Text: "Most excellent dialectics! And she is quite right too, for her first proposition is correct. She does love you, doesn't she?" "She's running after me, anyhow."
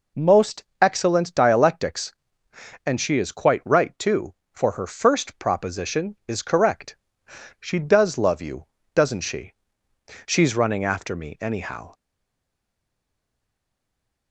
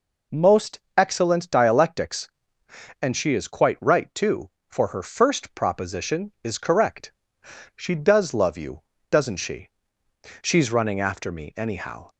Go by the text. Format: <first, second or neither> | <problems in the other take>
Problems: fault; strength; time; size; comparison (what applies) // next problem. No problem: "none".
second | pauses between "Most" and "excellent"; slight; at 0.6 s; 0.18 s long; slight in the second // stays silent after the last word; from 11.9 s on; 2.4 s long